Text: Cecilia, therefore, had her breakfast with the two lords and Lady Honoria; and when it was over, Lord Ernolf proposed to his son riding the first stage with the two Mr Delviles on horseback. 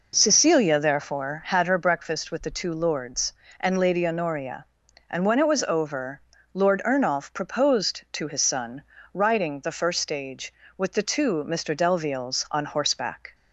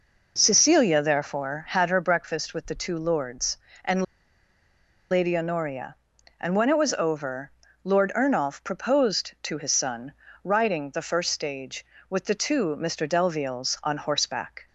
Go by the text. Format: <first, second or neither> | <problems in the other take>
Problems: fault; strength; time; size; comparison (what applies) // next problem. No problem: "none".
first | pauses between "and" and "Lady"; at 4.0 s; 1.0 s long // pauses between "son" and "riding"; slight; at 10.1 s; 0.32 s long; slight in the first